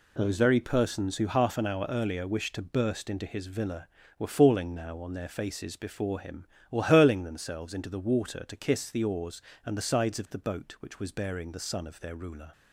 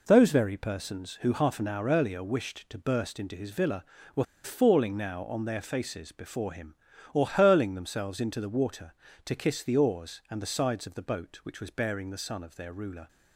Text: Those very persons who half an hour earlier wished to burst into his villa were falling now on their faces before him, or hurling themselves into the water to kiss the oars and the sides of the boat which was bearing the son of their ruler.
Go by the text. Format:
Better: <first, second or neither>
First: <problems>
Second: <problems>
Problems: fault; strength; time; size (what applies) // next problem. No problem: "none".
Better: first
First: none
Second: pauses between "were" and "falling"; slight; at 4.2 s; 0.20 s long